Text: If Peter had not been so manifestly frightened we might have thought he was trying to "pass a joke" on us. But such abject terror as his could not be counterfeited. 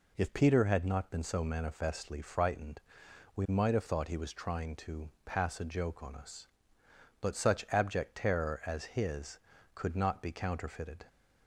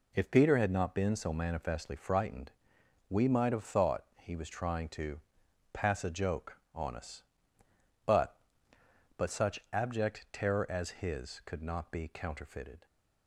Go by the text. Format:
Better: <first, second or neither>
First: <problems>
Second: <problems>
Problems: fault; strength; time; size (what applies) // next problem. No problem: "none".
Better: first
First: pauses between "frightened" and "we"; noticeable; at 2.7 s; 0.56 s long // pauses between "to" and "pass"; slight; at 5.1 s; 0.16 s long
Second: pauses between "frightened" and "we"; noticeable; at 2.5 s; 0.58 s long // pauses between "thought" and "he"; slight; at 4.0 s; 0.18 s long // pauses between "to" and "pass"; noticeable; at 5.2 s; 0.52 s long // says "But" twice; at 9.1 s